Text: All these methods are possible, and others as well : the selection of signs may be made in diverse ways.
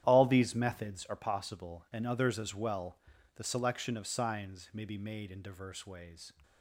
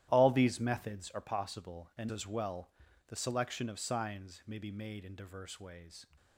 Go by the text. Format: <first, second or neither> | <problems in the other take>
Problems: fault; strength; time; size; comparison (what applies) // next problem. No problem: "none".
first | starts louder than the rest; strong; until 1.1 s; 13 dB; strong in the first // skips "others"; at 2.1 s